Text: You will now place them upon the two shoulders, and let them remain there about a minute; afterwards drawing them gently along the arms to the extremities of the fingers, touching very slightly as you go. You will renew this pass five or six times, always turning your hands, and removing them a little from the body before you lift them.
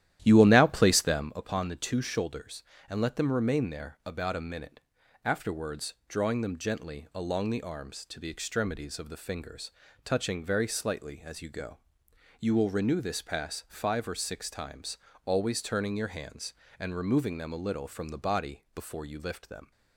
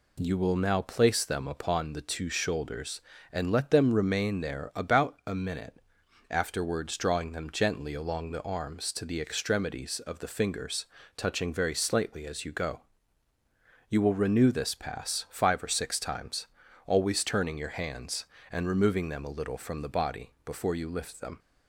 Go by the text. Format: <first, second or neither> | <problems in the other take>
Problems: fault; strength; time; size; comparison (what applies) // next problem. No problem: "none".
second | starts louder than the rest; strong; until 1.3 s; 12.5 dB